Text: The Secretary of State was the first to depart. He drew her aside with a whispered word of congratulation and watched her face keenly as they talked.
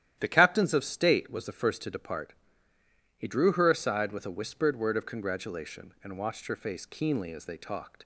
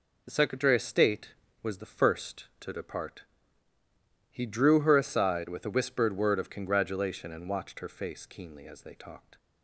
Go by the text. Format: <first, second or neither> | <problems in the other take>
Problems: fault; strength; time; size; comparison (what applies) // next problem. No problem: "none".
second | starts louder than the rest; strong; until 1.1 s; 11.5 dB // says "Captains" for "Secretary"; at 0.2 s